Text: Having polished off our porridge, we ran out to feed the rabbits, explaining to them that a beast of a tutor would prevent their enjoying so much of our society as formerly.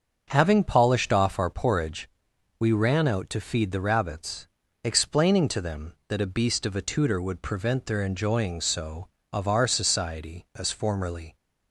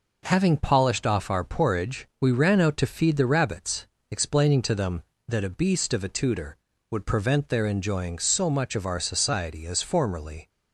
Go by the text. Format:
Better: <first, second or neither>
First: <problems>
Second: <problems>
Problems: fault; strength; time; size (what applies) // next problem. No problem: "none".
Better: second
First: starts louder than the rest; until 1.2 s; 6.5 dB // skips "much"; at 9.2 s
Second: none